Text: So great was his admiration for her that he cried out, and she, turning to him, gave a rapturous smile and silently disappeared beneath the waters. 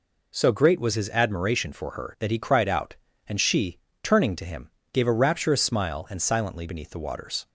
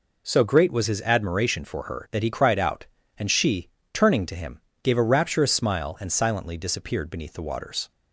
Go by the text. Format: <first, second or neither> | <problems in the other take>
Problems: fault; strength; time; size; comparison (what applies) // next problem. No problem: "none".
second | skips "disappeared"; at 6.6 s